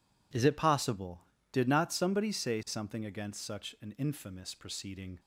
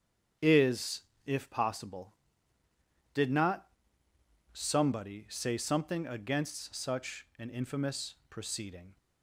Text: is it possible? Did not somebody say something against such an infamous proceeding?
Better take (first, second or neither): first